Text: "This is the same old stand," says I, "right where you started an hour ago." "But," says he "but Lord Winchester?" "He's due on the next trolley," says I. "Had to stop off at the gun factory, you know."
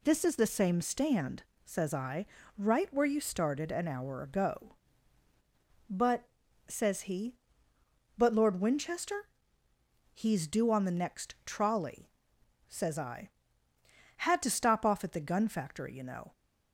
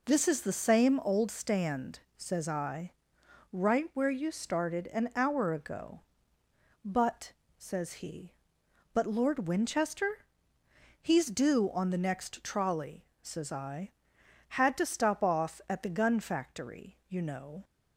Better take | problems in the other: second | skips "old"; at 0.8 s

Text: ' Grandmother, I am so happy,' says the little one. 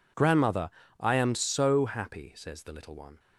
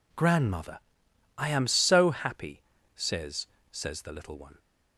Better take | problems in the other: first | says "says" twice; at 3.7 s

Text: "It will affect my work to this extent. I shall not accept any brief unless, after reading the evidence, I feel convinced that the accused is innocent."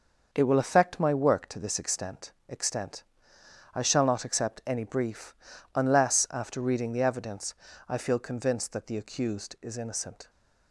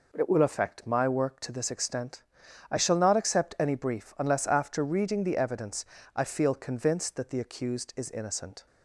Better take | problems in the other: second | starts louder than the rest; until 1.3 s; 6 dB // says "extent" twice; at 2.4 s // pauses between "brief" and "unless"; at 5.3 s; 0.42 s long

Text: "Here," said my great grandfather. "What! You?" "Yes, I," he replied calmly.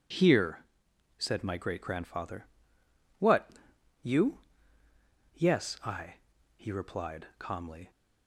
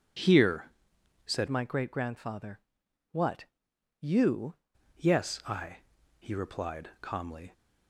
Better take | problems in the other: first | changes voice from "my" to "You"; from 1.4 to 4.5 s; 3.1 s long

